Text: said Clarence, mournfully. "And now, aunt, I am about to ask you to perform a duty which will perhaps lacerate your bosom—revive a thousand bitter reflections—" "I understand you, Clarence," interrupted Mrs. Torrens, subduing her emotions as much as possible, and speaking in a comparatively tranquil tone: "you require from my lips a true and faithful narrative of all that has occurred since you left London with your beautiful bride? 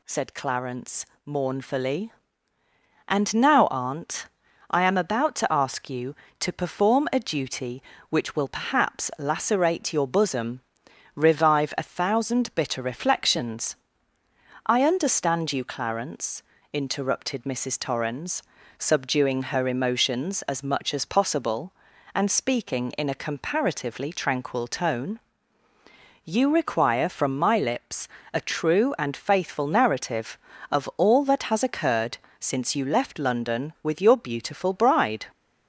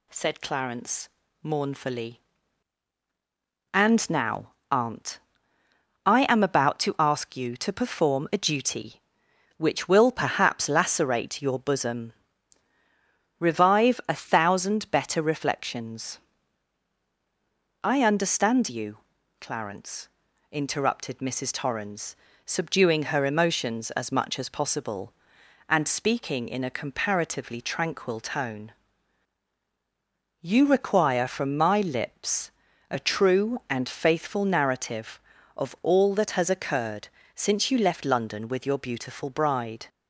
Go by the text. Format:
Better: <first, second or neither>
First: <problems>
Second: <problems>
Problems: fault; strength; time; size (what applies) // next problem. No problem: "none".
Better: first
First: pauses between "lips" and "a"; slight; at 28.0 s; 0.26 s long // pauses between "occurred" and "since"; slight; at 32.1 s; 0.20 s long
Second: says "better" for "bitter"; at 14.9 s // pauses between "lips" and "a"; slight; at 32.5 s; 0.36 s long // pauses between "occurred" and "since"; slight; at 37.0 s; 0.26 s long